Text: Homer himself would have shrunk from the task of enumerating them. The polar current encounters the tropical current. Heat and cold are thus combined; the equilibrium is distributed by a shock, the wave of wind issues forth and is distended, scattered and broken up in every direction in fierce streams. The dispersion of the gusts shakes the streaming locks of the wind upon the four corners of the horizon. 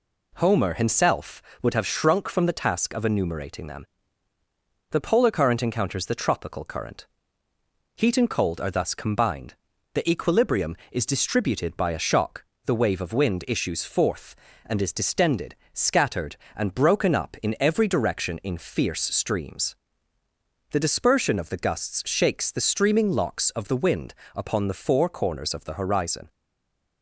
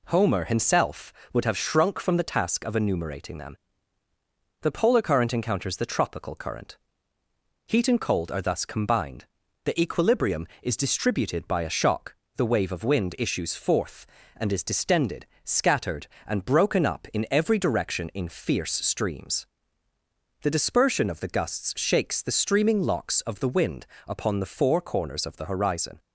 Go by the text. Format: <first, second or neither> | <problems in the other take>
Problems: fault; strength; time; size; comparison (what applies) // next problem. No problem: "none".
second | pauses between "wind" and "upon"; slight; at 24.1 s; 0.20 s long; slight in the second // stays silent after the last word; slight; from 26.3 s on; 0.7 s long